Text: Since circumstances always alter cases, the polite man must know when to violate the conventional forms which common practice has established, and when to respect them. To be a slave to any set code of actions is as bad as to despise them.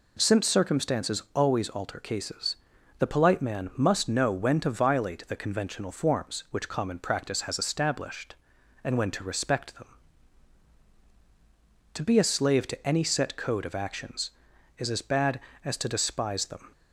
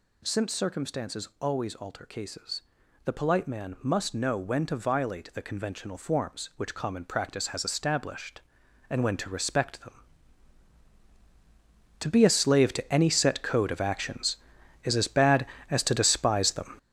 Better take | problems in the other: first | gets louder; strong; throughout; 8 dB

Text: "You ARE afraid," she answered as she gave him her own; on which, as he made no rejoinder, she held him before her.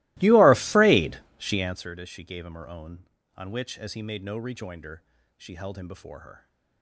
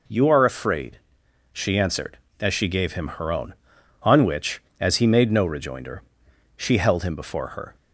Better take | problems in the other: second | starts louder than the rest; strong; until 1.8 s; 20.5 dB

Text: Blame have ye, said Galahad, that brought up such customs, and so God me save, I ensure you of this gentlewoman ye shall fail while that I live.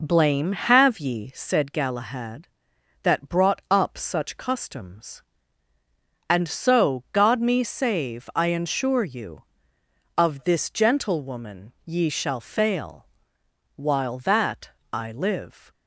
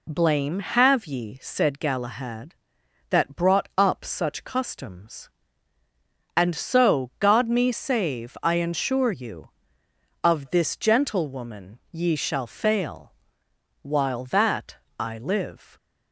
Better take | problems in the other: second | starts louder than the rest; noticeable; until 1.4 s; 4.5 dB // pauses between "fail" and "while"; noticeable; at 13.0 s; 0.68 s long; noticeable in the second // pauses between "that" and "I"; slight; at 14.6 s; 0.20 s long; slight in the second

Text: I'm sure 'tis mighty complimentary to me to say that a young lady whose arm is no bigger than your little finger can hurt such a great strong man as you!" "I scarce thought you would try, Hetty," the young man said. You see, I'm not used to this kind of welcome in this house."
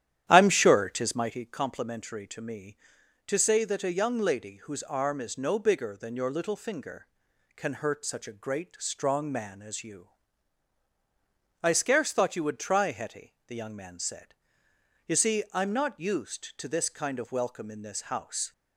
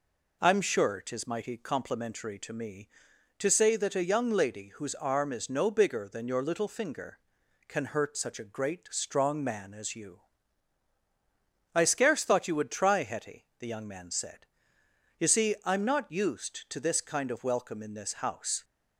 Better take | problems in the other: second | starts louder than the rest; strong; until 1.4 s; 11 dB

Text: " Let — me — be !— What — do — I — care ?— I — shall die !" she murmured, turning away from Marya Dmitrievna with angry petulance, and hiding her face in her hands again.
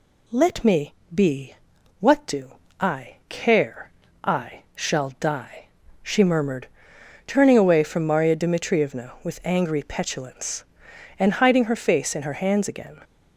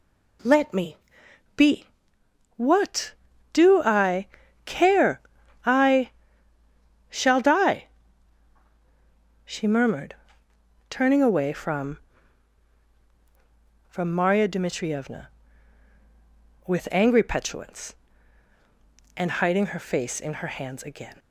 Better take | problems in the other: first | says "from" twice; at 13.9 s

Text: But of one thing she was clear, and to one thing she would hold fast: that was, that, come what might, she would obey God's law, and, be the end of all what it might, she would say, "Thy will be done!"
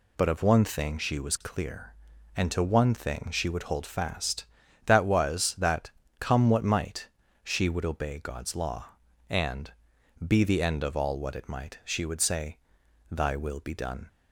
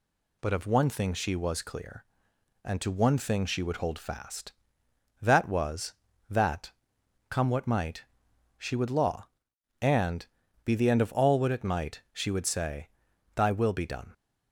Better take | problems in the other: first | skips "obey God's"; at 8.9 s

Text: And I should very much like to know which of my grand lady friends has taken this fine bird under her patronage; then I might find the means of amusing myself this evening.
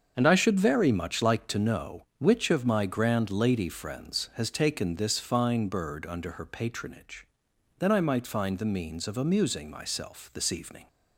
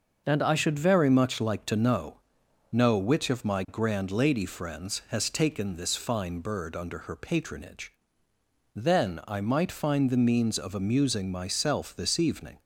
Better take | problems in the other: first | starts louder than the rest; noticeable; until 1.2 s; 6 dB; also in the first // says "know" twice; at 2.7 s

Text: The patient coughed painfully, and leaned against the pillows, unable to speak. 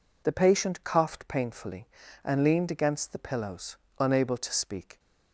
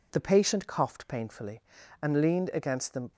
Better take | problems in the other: first | stops before "pillows unable to speak"; at 3.1 s

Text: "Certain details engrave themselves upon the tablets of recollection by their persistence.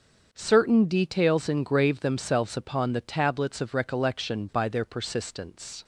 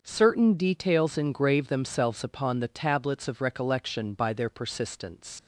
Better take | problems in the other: first | starts louder than the rest; until 1.0 s; 6.5 dB; also in the first // leaves "persistence" unfinished; at 5.3 s; 95 ms

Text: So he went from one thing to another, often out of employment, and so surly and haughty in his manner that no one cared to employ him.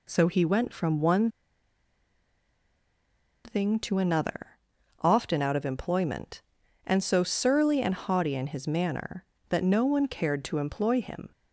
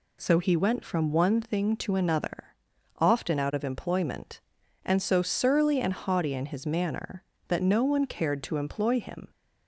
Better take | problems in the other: second | pauses between "one" and "thing"; strong; at 1.2 s; 2.1 s long

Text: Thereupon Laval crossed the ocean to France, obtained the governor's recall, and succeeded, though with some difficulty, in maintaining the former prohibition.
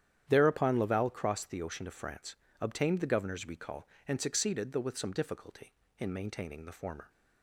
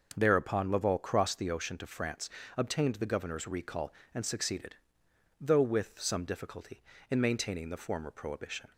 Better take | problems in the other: second | starts louder than the rest; strong; until 1.3 s; 10 dB; noticeable in the second // stops before "prohibition"; at 7.0 s

